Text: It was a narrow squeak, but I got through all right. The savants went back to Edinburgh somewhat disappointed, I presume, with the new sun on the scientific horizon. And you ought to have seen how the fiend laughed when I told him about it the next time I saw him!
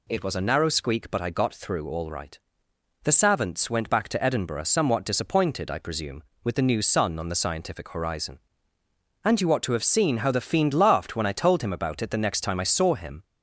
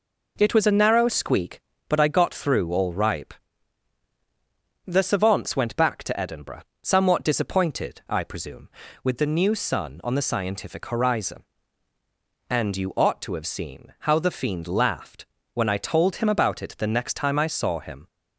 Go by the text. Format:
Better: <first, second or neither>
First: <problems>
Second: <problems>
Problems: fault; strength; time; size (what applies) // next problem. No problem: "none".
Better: first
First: none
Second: says "ripe" for "right"; at 2.9 s // pauses between "Edinburgh" and "somewhat"; slight; at 6.6 s; 0.20 s long // pauses between "laughed" and "when"; slight; at 15.2 s; 0.28 s long